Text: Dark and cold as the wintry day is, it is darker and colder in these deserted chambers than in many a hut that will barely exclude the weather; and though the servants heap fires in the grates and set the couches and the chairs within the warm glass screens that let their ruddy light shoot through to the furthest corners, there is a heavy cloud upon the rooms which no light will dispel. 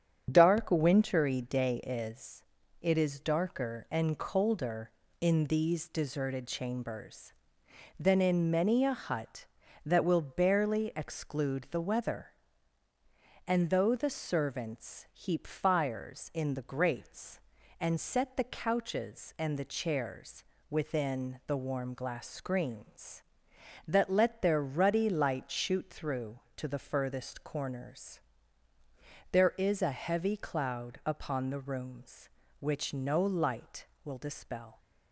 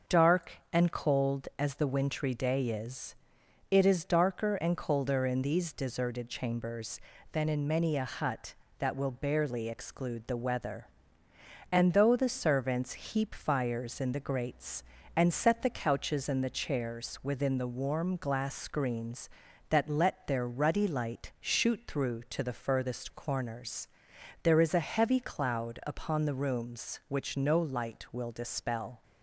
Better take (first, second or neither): second